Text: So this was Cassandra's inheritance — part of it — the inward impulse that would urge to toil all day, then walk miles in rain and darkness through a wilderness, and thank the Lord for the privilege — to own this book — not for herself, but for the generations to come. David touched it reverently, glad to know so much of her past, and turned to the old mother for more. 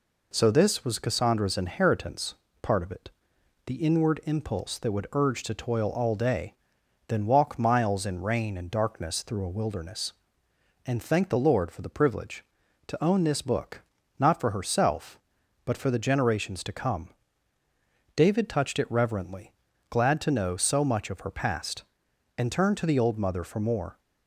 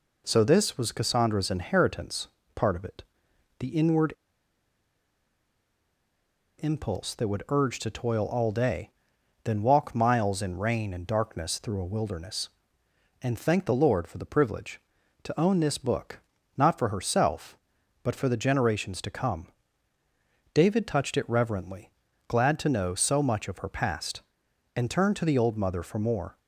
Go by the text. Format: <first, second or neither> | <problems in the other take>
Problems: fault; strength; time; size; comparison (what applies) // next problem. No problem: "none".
first | pauses between "inward" and "impulse"; strong; at 4.1 s; 2.4 s long